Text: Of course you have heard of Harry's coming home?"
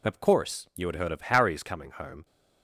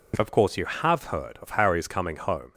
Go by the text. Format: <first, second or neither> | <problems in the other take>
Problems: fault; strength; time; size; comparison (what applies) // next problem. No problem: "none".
second | says "had" for "have"; at 0.8 s